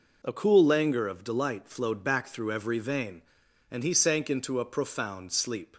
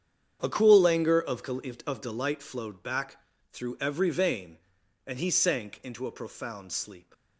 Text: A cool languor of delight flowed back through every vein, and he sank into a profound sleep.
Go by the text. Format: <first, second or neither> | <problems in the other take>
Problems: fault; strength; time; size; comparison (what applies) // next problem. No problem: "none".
first | starts louder than the rest; strong; until 1.4 s; 9 dB // says "of" twice; at 1.8 s // pauses between "back" and "through"; slight; at 3.1 s; 0.36 s long